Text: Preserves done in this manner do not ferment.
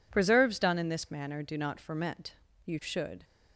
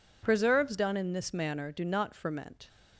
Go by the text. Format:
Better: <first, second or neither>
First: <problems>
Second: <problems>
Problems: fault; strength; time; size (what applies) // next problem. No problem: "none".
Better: second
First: goes on to say "You should"; from 2.6 s on; 0.57 s long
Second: none